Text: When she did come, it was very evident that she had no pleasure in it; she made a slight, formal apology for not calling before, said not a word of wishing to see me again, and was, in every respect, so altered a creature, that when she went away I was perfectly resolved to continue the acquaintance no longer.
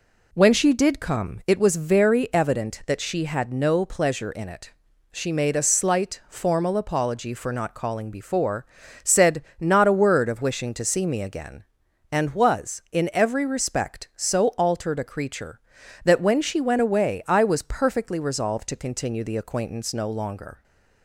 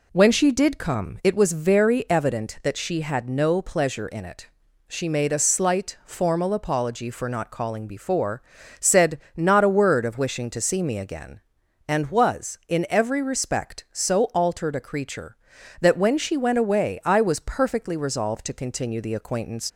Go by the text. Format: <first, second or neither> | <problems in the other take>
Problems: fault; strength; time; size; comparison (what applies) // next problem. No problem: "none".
first | pauses between "said" and "not"; slight; at 9.2 s; 0.16 s long; slight in the first // stops before "no longer"; at 19.7 s